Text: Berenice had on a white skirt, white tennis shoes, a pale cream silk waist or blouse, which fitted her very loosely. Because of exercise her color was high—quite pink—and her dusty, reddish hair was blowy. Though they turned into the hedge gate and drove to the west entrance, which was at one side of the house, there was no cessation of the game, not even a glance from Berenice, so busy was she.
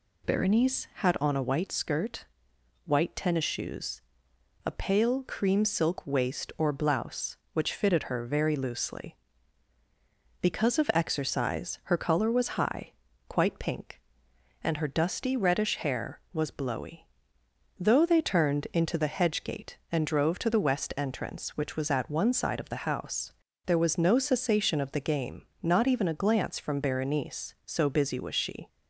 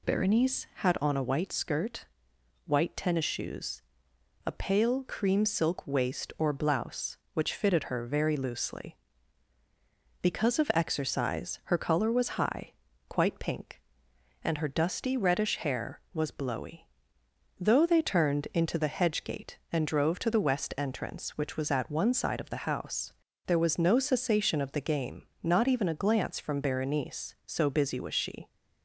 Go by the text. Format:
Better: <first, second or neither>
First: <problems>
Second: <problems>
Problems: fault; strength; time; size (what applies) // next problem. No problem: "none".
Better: neither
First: none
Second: none